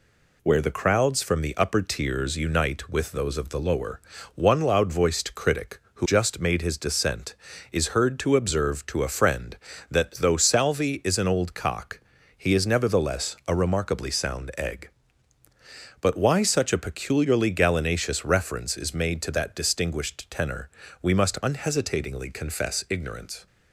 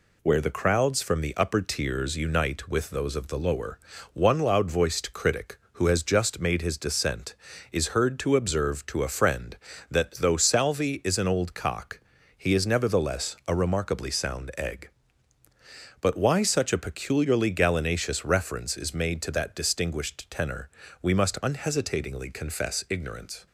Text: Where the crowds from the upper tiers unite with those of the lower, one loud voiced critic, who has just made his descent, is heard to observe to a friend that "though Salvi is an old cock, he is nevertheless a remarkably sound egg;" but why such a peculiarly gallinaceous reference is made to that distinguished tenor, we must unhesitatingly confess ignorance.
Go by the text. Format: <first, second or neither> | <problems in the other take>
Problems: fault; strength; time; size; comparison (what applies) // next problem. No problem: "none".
second | skips "has"; at 6.0 s